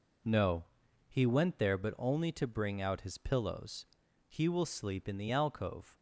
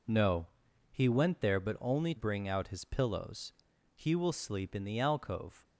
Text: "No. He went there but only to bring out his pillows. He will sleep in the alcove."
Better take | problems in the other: first | skips "to"; at 2.1 s

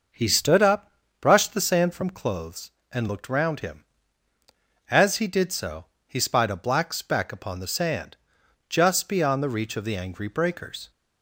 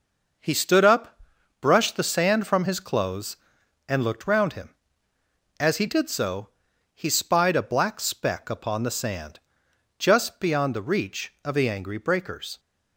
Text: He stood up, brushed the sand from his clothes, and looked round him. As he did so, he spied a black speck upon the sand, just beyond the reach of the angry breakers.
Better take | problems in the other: second | starts louder than the rest; noticeable; until 1.4 s; 6 dB // skips "his"; at 2.1 s

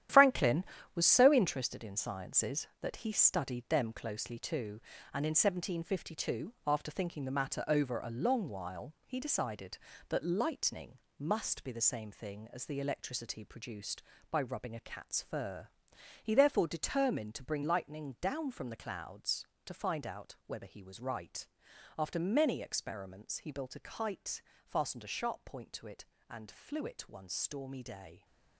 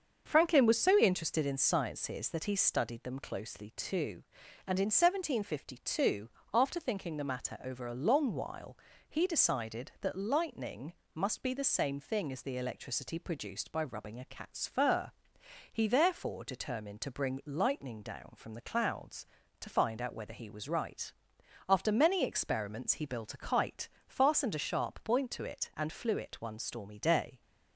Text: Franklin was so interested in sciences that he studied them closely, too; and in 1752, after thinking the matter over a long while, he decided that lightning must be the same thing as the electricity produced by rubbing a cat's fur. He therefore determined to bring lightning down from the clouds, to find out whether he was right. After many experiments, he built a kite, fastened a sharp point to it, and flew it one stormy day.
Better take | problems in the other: second | gets quieter; strong; throughout; 10 dB // starts louder than the rest; strong; until 1.4 s; 11 dB; also in the second // pauses between "lightning" and "must"; slight; at 10.9 s; 0.18 s long; slight in the second

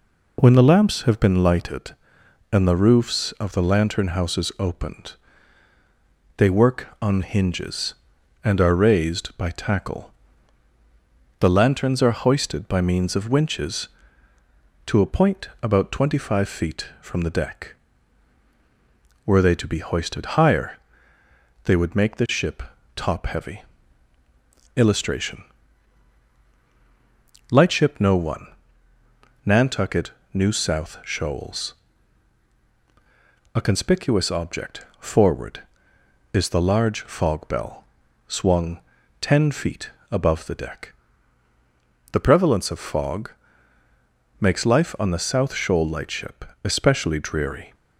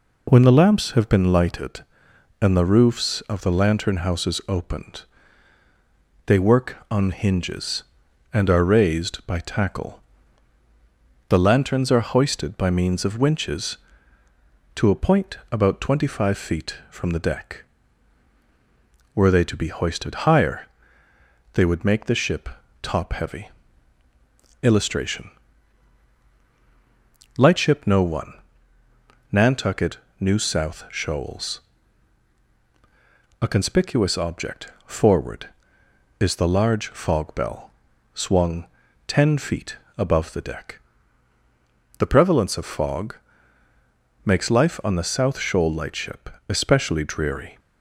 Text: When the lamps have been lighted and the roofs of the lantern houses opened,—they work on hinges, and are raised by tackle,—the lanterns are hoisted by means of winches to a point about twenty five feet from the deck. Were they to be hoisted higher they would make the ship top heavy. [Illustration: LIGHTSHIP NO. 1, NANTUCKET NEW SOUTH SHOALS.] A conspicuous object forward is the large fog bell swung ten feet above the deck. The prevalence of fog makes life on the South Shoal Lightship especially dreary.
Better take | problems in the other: neither | pauses between "higher" and "they"; noticeable; the same in both // pauses between "ship" and "top"; slight; the same in both // pauses between "NANTUCKET" and "NEW"; slight; the same in both // pauses between "bell" and "swung"; the same in both // pauses between "swung" and "ten"; the same in both // pauses between "feet" and "above"; slight; the same in both // pauses between "fog" and "makes"; the same in both // pauses between "Lightship" and "especially"; slight; the same in both

